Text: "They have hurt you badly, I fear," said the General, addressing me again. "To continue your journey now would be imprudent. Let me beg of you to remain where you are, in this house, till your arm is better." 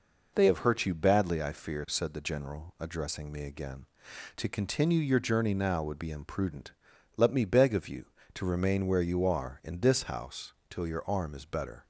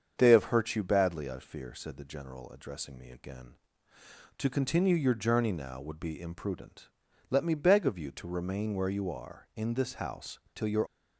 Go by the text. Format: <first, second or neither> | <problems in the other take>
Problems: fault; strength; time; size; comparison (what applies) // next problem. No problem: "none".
first | starts louder than the rest; strong; until 1.1 s; 7 dB // stops before "arm is better"; at 10.8 s